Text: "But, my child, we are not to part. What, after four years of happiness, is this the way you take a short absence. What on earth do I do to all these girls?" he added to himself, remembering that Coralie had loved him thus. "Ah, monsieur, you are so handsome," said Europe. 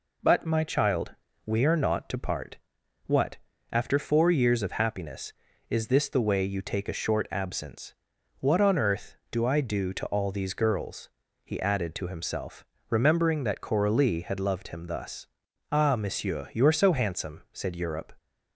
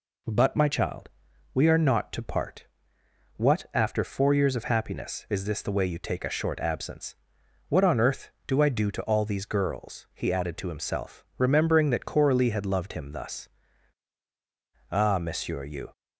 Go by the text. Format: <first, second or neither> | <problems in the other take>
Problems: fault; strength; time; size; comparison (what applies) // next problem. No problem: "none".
first | stops before "are so handsome said Europe"; at 15.9 s